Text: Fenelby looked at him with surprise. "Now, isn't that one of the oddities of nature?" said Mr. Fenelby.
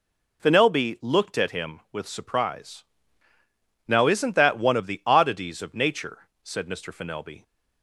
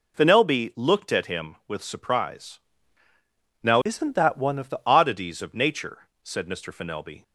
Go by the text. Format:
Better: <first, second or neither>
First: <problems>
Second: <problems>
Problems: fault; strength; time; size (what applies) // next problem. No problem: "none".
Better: first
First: none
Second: changes voice from "isn't" to "the"; from 3.8 to 4.7 s; 0.9 s long